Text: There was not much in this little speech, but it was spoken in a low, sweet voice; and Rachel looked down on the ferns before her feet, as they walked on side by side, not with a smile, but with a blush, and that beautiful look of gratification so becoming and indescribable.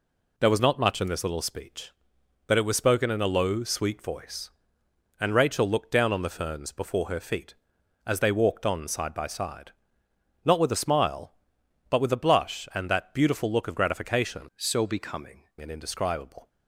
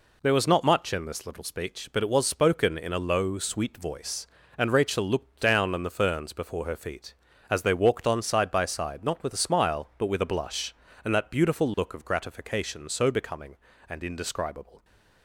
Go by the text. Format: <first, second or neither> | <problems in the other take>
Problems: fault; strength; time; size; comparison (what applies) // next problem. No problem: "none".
second | changes voice from "so" to "becoming"; from 14.5 to 15.4 s; 0.9 s long